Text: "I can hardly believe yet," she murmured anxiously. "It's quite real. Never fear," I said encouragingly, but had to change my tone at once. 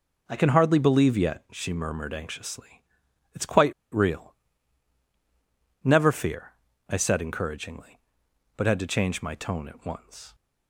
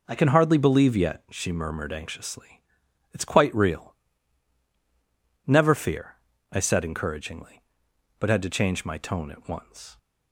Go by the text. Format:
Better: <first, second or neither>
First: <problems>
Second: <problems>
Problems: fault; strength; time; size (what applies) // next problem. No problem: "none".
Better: second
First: pauses between "quite" and "real"; slight; at 3.7 s; 0.19 s long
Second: none